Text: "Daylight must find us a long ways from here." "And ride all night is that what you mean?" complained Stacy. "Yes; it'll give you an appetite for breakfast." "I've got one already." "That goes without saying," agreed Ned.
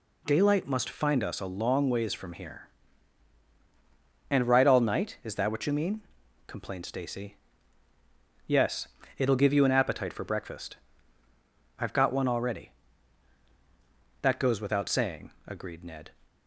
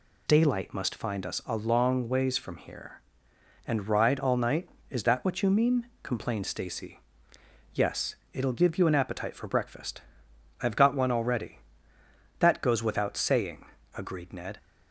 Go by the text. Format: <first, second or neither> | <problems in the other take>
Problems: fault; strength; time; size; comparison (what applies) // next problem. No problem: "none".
neither | none